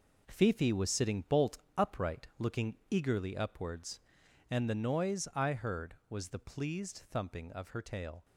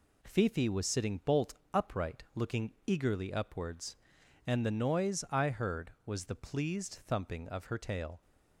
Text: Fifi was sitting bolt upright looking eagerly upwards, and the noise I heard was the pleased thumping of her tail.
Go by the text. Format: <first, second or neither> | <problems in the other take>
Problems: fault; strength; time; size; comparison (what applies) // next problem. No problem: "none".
second | gets quieter; strong; throughout; 8 dB // pauses between "bolt" and "upright"; slight; at 1.5 s; 0.18 s long; slight in the second